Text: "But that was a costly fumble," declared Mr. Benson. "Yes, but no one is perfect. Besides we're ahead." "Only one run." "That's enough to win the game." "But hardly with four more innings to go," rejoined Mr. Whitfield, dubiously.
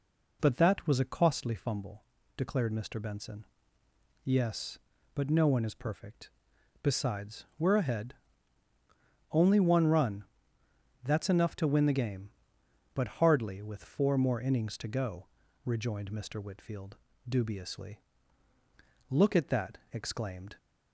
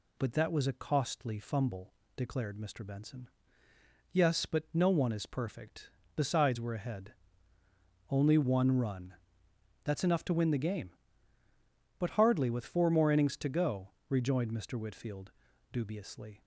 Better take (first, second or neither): second